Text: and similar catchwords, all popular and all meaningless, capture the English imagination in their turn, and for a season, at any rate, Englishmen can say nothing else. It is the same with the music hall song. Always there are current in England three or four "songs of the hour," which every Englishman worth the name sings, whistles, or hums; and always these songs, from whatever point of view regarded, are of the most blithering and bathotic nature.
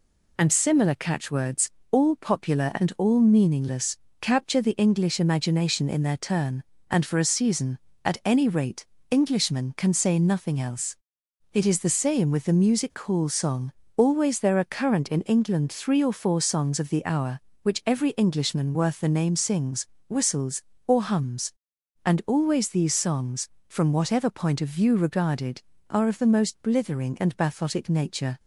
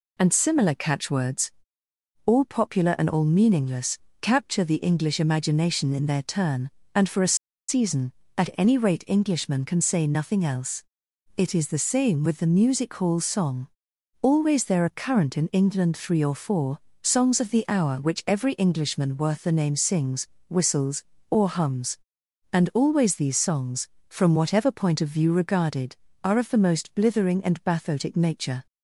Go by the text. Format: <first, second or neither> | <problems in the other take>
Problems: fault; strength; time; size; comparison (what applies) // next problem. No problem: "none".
first | pauses between "a" and "season"; slight; at 7.3 s; 0.33 s long // pauses between "four" and "songs"; slight; at 16.7 s; 0.24 s long